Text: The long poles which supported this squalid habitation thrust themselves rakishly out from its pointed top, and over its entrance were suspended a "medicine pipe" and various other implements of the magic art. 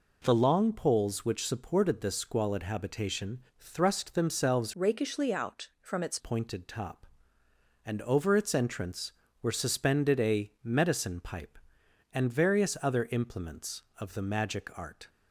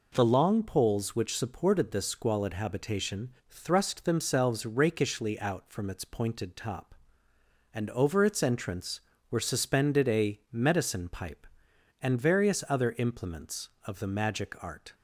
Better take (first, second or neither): second